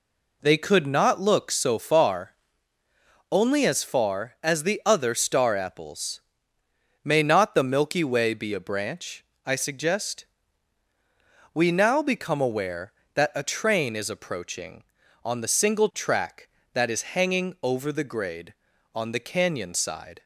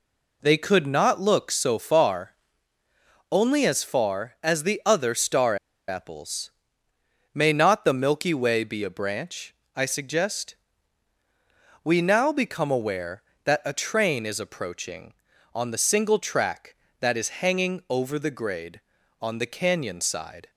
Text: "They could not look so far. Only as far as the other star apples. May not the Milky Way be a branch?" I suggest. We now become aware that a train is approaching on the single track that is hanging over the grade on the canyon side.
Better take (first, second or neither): first